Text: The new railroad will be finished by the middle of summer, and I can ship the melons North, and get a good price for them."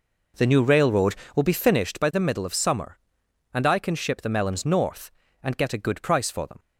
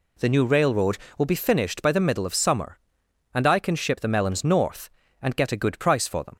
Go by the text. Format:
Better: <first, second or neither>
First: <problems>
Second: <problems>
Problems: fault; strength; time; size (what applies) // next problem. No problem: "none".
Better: second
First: starts louder than the rest; noticeable; until 1.9 s; 5 dB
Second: none